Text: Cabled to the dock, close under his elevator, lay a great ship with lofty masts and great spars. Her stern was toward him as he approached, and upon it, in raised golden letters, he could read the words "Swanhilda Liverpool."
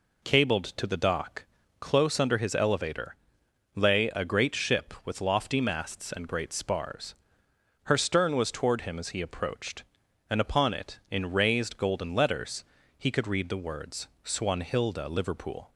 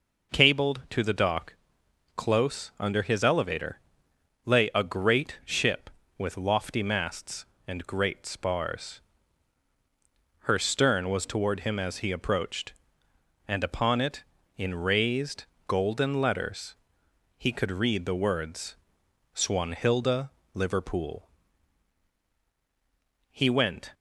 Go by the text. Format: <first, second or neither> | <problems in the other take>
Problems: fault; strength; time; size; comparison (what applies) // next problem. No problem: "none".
first | pauses between "raised" and "golden"; slight; at 15.4 s; 0.24 s long // pauses between "words" and "Swanhilda"; noticeable; at 18.7 s; 0.58 s long // pauses between "Swanhilda" and "Liverpool"; slight; at 20.2 s; 0.24 s long // goes on to say "He went"; noticeable; from 23.3 s on; 0.62 s long